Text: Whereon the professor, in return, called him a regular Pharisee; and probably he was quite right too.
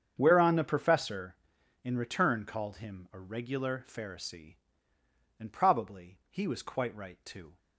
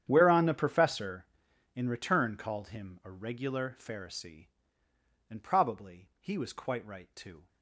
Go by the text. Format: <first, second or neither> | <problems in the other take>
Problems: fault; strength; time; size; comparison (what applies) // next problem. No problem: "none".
first | gets quieter; strong; throughout; 18.5 dB // starts louder than the rest; strong; until 1.0 s; 9.5 dB; strong in the first